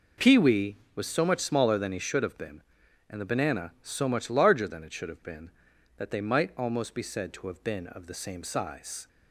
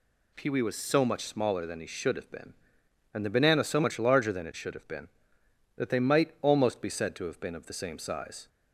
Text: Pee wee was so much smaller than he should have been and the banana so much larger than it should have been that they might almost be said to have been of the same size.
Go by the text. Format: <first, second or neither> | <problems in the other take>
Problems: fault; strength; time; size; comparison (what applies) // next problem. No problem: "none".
neither | none